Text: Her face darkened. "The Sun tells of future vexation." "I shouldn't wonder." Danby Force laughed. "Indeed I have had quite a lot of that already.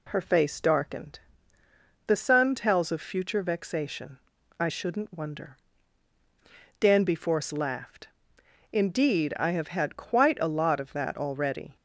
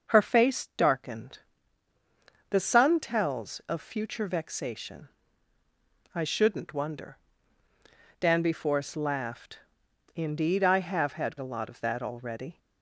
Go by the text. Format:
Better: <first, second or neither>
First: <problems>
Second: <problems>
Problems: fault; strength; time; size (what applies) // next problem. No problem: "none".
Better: first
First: none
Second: starts louder than the rest; noticeable; until 1.1 s; 6 dB // skips "quite"; at 11.3 s